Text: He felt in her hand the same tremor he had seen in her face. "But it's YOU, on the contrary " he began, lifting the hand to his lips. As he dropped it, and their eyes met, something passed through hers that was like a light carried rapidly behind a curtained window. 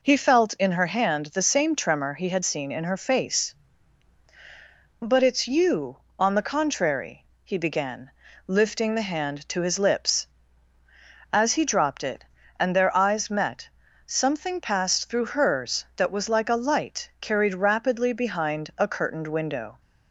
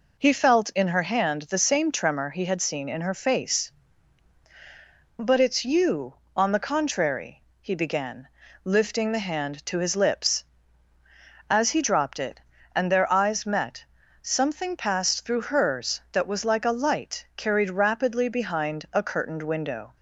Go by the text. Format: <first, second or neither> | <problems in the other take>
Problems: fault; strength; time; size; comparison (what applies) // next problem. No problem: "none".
neither | none